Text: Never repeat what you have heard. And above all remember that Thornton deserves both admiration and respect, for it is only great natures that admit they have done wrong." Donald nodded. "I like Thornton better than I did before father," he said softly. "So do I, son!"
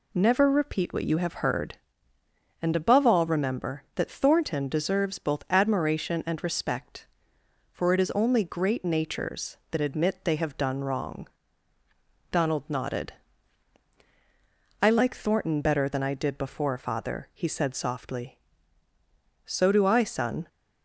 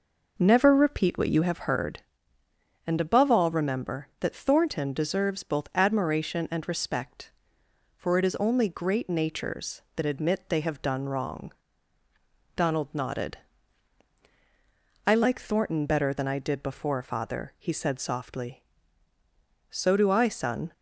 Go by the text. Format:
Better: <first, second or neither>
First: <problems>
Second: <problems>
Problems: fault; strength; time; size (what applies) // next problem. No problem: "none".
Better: first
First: none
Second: starts louder than the rest; noticeable; until 1.7 s; 5 dB